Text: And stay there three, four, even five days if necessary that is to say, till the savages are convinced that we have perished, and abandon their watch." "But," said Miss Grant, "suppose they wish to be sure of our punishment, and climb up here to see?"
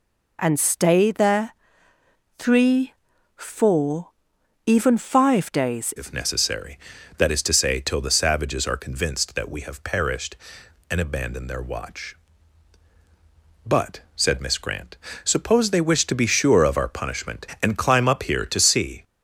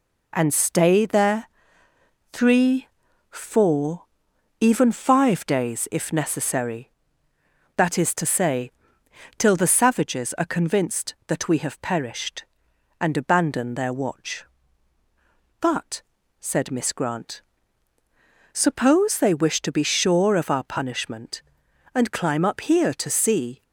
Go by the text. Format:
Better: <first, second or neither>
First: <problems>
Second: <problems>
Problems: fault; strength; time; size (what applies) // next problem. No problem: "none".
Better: second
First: pauses between "there" and "three"; noticeable; at 1.5 s; 0.86 s long // changes voice at "if"; from 5.9 s on; 13.1 s long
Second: pauses between "there" and "three"; noticeable; at 1.4 s; 0.86 s long